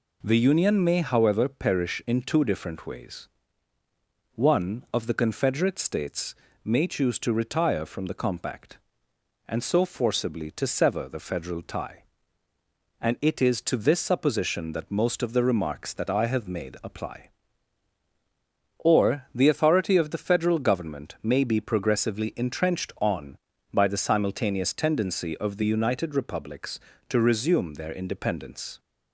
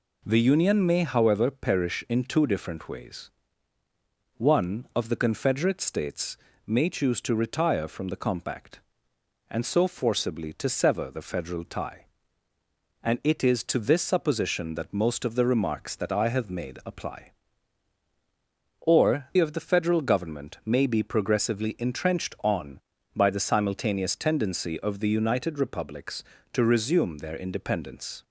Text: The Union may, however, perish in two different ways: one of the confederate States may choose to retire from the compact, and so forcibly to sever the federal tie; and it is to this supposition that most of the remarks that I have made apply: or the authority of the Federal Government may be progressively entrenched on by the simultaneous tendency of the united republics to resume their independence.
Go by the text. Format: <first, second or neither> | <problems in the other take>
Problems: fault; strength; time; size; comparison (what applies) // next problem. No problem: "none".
first | pauses between "States" and "may"; slight; at 6.3 s; 0.30 s long; slight in the first // skips "the authority"; at 19.3 s